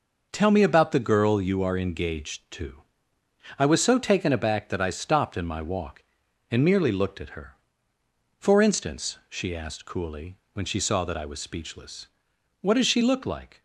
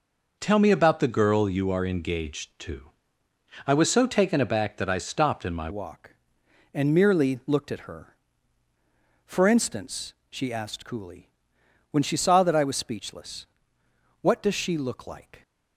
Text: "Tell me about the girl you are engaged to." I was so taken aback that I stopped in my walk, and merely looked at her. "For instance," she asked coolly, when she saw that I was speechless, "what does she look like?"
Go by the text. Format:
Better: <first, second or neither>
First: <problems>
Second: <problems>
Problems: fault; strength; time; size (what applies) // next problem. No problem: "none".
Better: first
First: none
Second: changes voice at "walk"; from 5.7 s on; 9.7 s long